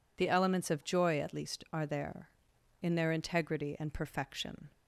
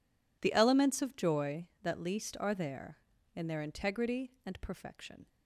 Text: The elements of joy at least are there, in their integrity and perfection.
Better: first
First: none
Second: says "that" for "at"; at 1.8 s

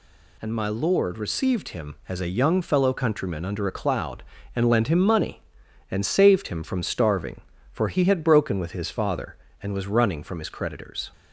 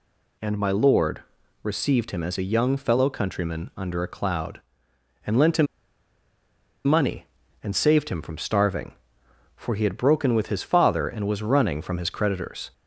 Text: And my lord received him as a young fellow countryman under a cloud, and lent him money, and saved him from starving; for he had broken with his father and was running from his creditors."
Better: first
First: none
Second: pauses between "lord" and "received"; at 1.2 s; 0.40 s long // pauses between "him" and "money"; at 5.6 s; 1.1 s long

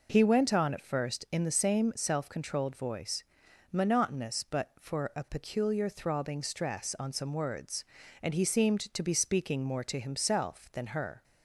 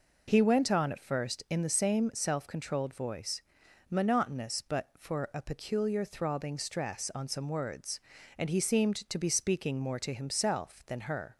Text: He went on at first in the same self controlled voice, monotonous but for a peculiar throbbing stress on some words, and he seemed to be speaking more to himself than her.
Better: neither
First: none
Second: none

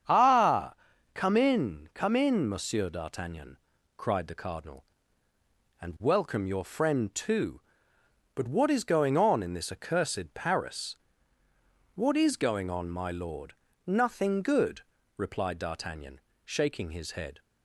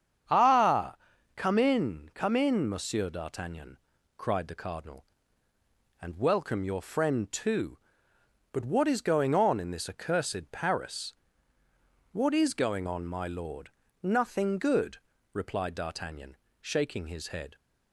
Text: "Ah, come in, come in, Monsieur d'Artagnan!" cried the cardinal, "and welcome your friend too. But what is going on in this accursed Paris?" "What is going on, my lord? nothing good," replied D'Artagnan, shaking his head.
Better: neither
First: starts louder than the rest; strong; until 1.4 s; 8 dB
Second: starts louder than the rest; strong; until 1.6 s; 8 dB

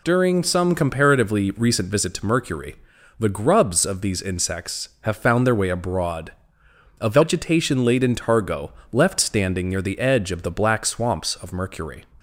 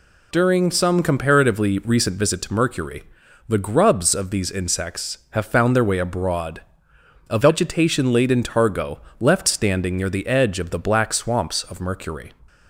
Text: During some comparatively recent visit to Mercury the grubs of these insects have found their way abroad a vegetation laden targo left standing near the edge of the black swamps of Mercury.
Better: neither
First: pauses between "Mercury" and "the"; at 2.7 s; 0.44 s long // pauses between "abroad" and "a"; noticeable; at 6.3 s; 0.68 s long // pauses between "targo" and "left"; slight; at 8.7 s; 0.20 s long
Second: pauses between "Mercury" and "the"; noticeable; at 3.0 s; 0.46 s long // pauses between "abroad" and "a"; noticeable; at 6.6 s; 0.68 s long // pauses between "targo" and "left"; slight; at 8.9 s; 0.20 s long

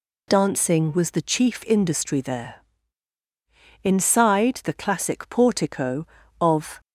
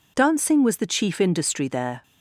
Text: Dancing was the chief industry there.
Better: second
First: goes on to say "Inside the classic portico of"; strong; from 3.8 s on; 2.9 s long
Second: none

